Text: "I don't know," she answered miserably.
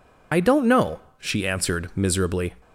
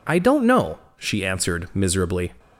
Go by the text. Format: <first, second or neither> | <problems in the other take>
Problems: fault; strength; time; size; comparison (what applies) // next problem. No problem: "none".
second | loses the start of "I"; at 0.3 s; 45 ms